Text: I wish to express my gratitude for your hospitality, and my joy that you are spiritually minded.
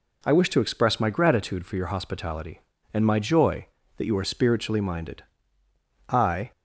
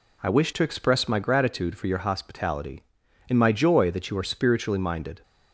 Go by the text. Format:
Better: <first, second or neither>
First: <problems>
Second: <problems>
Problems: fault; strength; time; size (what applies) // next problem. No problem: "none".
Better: second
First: goes on to say "I"; slight; from 6.0 s on; 0.42 s long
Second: none